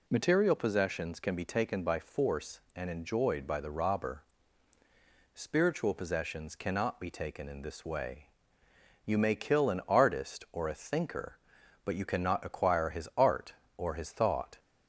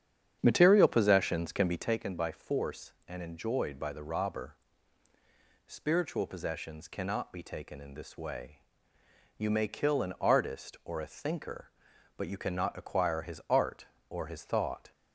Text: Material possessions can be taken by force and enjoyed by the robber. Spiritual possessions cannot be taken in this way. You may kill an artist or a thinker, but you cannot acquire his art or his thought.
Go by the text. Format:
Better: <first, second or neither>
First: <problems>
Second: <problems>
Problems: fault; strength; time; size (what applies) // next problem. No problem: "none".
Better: first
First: none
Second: starts louder than the rest; strong; until 2.0 s; 8.5 dB